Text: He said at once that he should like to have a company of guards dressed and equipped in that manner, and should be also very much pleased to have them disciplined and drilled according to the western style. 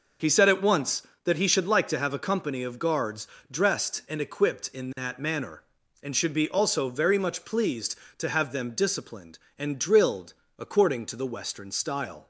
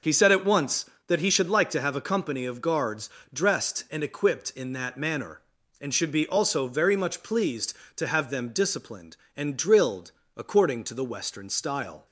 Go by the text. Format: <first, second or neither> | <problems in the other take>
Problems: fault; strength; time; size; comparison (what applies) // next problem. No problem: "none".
neither | pauses between "guards" and "dressed"; slight; the same in both // pauses between "drilled" and "according"; slight; the same in both